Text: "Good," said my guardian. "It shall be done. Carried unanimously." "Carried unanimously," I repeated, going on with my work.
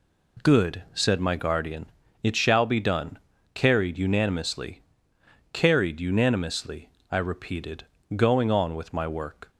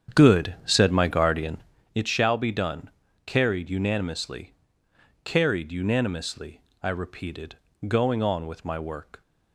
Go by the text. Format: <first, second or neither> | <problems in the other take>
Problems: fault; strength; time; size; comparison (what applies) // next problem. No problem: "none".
first | starts louder than the rest; strong; until 1.9 s; 8.5 dB